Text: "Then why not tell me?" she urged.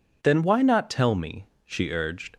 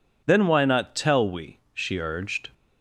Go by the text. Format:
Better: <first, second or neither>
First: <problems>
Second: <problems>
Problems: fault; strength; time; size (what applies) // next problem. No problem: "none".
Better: first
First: none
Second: says "we" for "me"; at 1.2 s